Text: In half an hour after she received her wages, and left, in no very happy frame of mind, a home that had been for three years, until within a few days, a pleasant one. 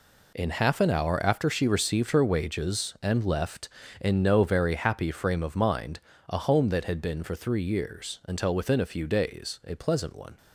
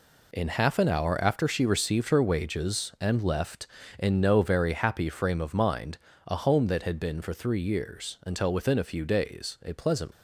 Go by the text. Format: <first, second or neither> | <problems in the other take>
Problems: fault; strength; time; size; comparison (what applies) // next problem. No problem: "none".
first | stops before "one"; at 10.1 s